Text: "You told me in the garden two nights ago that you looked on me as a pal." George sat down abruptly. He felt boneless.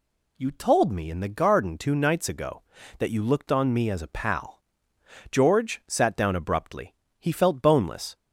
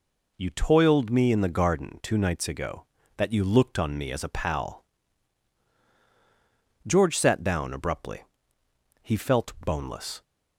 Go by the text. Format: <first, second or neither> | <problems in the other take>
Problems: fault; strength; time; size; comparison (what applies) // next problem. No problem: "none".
first | says "toiled" for "told"; at 0.4 s